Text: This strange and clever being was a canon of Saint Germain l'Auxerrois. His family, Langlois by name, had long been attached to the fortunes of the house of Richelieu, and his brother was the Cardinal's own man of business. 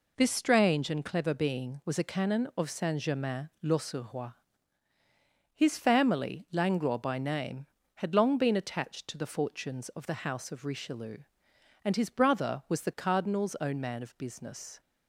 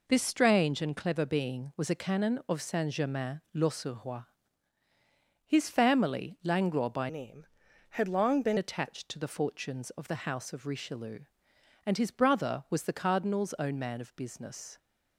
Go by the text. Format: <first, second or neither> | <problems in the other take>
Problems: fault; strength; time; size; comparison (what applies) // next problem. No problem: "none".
first | changes voice from "name" to "been"; from 7.0 to 8.5 s; 1.5 s long